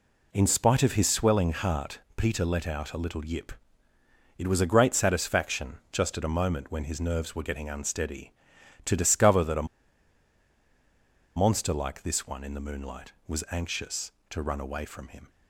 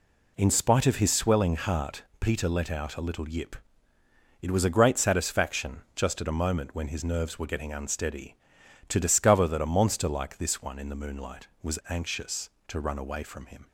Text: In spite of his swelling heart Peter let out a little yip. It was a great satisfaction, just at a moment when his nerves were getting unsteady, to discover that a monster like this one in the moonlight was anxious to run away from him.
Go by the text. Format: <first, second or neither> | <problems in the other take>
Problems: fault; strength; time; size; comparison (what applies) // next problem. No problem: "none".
second | pauses between "heart" and "Peter"; slight; at 1.9 s; 0.16 s long; slight in the second // pauses between "a" and "monster"; strong; at 9.6 s; 1.7 s long